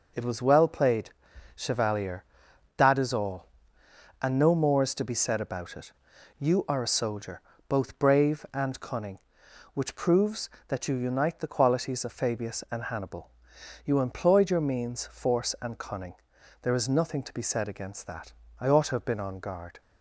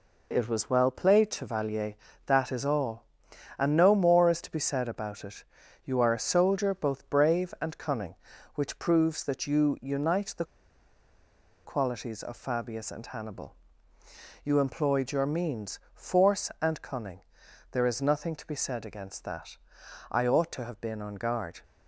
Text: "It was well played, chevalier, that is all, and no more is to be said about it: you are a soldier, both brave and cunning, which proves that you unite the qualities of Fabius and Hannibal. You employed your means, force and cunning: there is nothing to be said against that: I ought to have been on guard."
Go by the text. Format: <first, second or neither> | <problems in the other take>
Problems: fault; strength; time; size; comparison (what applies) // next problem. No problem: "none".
first | pauses between "the" and "qualities"; at 10.4 s; 1.2 s long